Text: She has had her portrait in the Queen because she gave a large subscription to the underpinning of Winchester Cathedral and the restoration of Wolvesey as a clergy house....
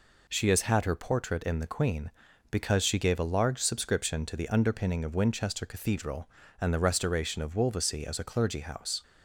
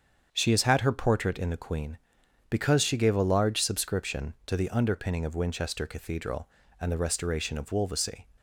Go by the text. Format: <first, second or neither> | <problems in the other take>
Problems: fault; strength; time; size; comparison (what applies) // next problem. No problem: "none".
first | starts louder than the rest; strong; until 1.3 s; 7.5 dB // stops before "as a clergy house"; at 8.3 s